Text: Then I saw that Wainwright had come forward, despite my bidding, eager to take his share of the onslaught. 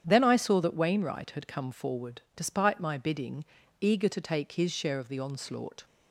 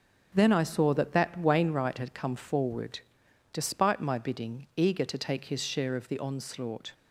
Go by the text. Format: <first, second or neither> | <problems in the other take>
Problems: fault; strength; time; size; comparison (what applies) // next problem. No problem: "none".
first | starts louder than the rest; strong; until 1.3 s; 7.5 dB; strong in the first // says "that" twice; at 1.1 s